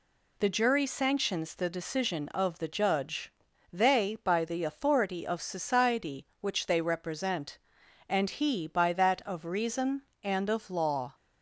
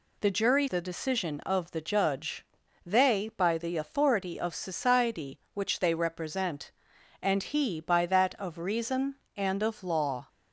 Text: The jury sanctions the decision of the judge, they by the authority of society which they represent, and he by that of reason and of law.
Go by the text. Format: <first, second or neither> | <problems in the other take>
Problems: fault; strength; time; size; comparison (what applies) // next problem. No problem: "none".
first | skips "sanctions"; at 0.6 s